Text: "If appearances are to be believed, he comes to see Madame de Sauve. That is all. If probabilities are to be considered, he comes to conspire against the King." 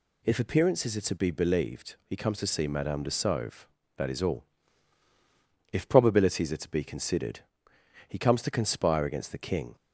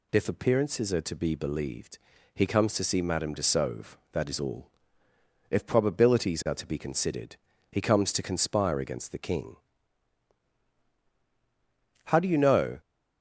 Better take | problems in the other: first | goes on to say "How do you know"; noticeable; from 12.0 s on; 0.74 s long

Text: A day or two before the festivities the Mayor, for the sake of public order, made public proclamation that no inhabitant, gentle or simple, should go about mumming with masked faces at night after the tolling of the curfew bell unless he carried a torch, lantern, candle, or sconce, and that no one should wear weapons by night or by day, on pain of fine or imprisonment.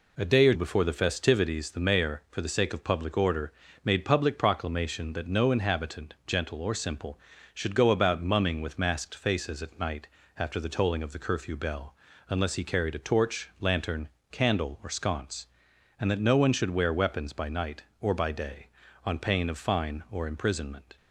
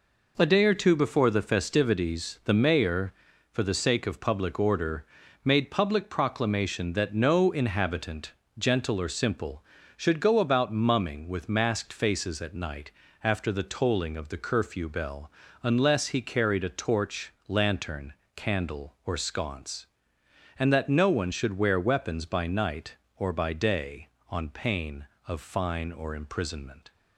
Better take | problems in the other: second | skips "two"; at 0.5 s // pauses between "night" and "after"; slight; at 10.0 s; 0.32 s long; slight in the second // pauses between "bell" and "unless"; slight; at 11.9 s; 0.32 s long; slight in the second

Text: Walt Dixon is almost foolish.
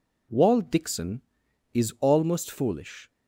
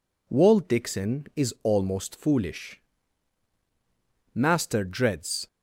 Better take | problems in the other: first | goes on to say "Master dreads"; noticeable; from 4.3 s on; 1.1 s long

